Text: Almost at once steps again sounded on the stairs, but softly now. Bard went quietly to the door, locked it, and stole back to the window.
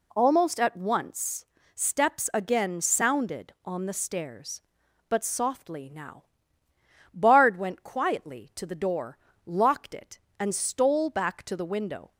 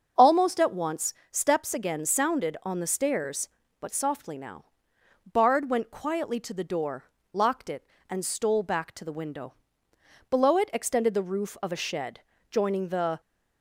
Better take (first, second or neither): first